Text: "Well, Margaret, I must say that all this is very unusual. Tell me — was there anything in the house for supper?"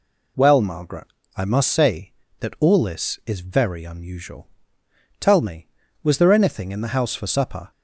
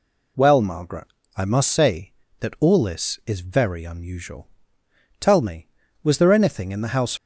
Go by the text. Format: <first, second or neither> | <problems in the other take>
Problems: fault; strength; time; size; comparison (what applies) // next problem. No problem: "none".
first | stops before "for supper"; at 7.1 s